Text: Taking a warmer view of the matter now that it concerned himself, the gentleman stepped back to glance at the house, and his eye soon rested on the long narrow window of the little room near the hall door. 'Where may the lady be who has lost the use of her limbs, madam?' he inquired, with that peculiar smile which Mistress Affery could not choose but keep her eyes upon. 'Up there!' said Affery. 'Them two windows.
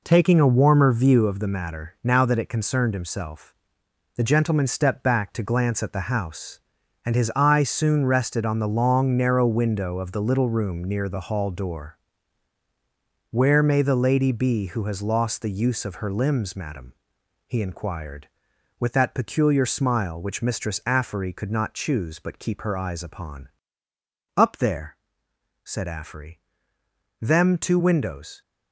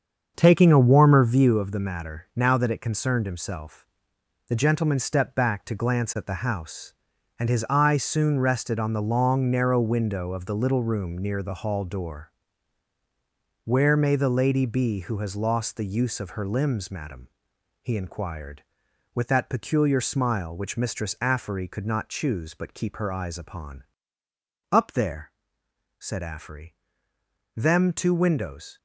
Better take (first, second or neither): first